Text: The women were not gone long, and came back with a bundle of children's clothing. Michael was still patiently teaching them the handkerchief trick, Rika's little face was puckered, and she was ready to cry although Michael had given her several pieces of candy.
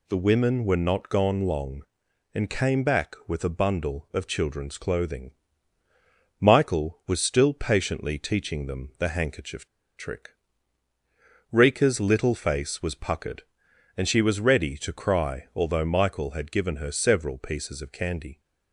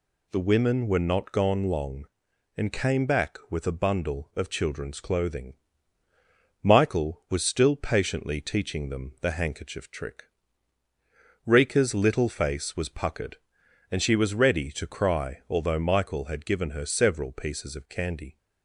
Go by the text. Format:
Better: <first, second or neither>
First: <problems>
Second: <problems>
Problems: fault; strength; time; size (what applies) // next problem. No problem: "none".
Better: second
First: pauses between "handkerchief" and "trick"; slight; at 9.6 s; 0.29 s long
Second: none